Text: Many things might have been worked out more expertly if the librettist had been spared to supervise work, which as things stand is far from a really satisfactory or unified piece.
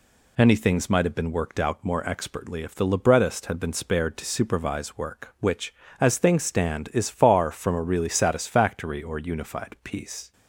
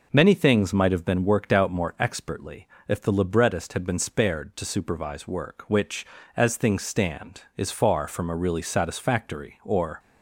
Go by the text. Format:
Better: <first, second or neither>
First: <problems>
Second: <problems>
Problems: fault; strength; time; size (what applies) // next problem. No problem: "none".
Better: first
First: none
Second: pauses between "expertly" and "if"; slight; at 2.6 s; 0.20 s long // stops before "unified piece"; at 9.9 s